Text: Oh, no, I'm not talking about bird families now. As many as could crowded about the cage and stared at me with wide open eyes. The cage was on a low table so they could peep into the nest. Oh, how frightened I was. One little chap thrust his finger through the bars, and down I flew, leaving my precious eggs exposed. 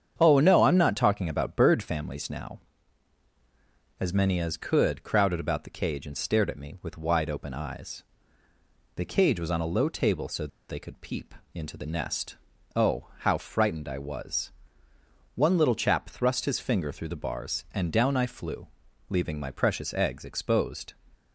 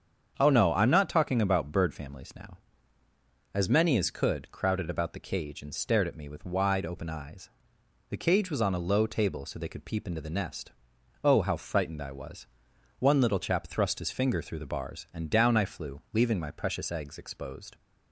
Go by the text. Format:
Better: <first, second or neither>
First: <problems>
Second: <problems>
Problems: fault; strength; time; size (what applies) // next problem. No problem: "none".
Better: second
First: starts louder than the rest; strong; until 1.1 s; 8 dB // pauses between "so" and "they"; slight; at 10.4 s; 0.22 s long // pauses between "peep" and "into"; slight; at 11.3 s; 0.22 s long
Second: starts louder than the rest; strong; until 1.3 s; 7.5 dB